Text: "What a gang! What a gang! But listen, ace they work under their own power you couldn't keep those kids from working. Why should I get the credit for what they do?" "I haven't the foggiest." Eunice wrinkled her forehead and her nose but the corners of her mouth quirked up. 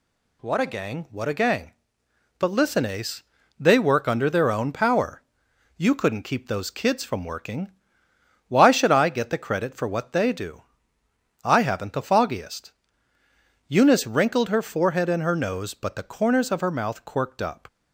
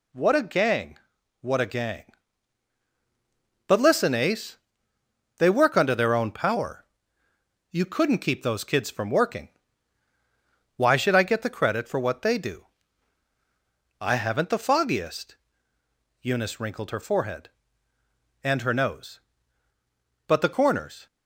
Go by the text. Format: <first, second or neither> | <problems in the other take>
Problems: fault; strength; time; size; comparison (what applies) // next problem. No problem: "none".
first | pauses between "ace" and "they"; noticeable; at 4.5 s; 0.80 s long; slight in the first // pauses between "power" and "you"; noticeable; at 6.8 s; 0.86 s long; noticeable in the first // stops before "of her mouth quirked up"; at 21.0 s